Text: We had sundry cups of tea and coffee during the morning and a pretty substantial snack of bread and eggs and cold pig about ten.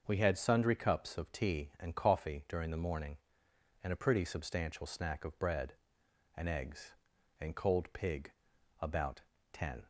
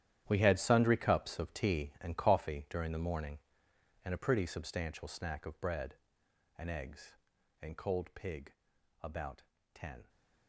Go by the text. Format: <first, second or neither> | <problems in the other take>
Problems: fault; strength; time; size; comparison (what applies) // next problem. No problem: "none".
first | gets quieter; strong; throughout; 13.5 dB // starts louder than the rest; strong; until 1.2 s; 11 dB; also in the first // pauses between "pig" and "about"; noticeable; at 8.5 s; 0.52 s long; noticeable in the first // pauses between "about" and "ten"; slight; at 9.4 s; 0.32 s long; slight in the first